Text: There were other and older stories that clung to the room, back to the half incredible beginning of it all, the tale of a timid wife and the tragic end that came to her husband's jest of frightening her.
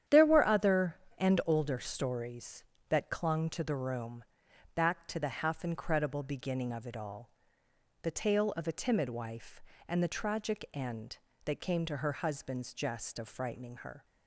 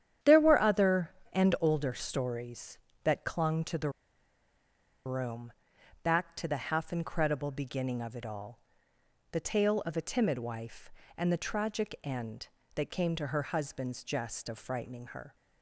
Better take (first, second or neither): first